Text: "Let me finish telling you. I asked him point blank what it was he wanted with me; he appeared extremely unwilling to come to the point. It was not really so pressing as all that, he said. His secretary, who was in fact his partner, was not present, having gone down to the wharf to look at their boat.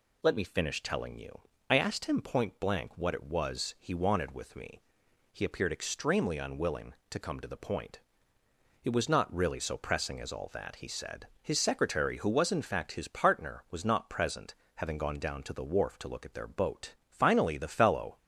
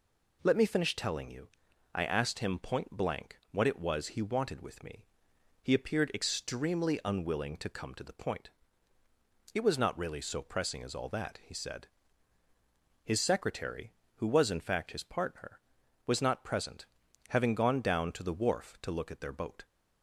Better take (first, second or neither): second